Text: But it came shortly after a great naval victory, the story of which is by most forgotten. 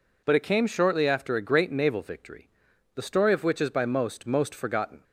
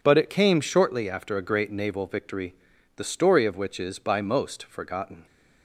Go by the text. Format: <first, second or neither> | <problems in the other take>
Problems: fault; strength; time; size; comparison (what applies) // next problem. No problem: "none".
second | says "most" twice; at 4.2 s